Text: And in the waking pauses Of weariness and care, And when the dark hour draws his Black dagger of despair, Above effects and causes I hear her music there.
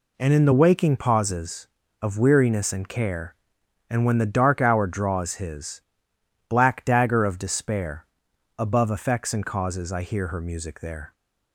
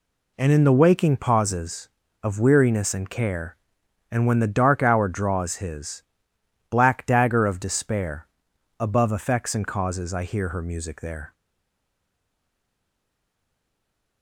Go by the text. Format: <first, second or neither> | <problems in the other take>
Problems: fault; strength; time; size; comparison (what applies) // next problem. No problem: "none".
first | pauses between "his" and "Black"; noticeable; at 6.0 s; 0.68 s long; noticeable in the first // stays silent after the last word; strong; from 11.3 s on; 2.9 s long